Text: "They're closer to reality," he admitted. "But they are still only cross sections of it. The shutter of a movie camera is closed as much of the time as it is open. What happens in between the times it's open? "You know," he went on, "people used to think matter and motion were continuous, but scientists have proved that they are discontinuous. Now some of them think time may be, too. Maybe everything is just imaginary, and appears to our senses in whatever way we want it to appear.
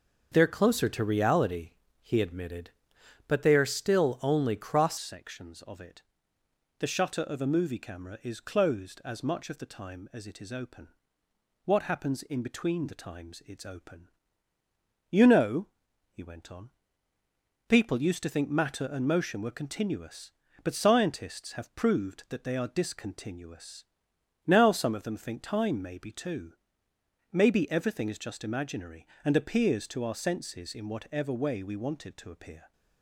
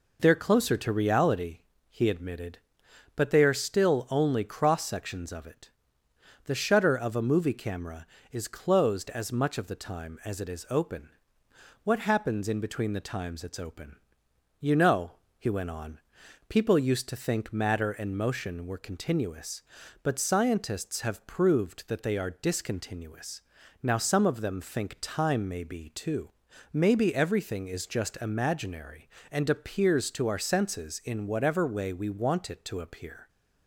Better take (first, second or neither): second